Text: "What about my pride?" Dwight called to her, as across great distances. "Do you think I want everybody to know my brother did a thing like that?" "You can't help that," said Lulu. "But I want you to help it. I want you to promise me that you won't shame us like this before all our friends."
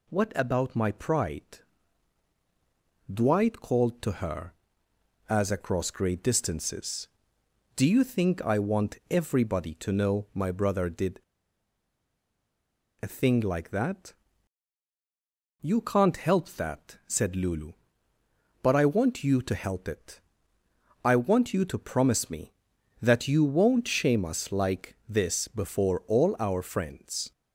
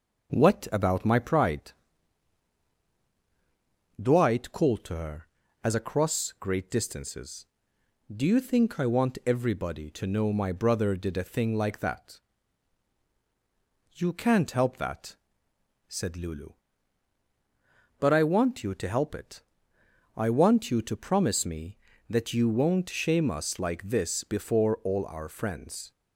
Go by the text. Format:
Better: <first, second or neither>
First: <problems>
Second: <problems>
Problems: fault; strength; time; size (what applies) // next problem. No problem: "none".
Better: second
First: pauses between "did" and "a"; strong; at 11.1 s; 1.8 s long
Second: none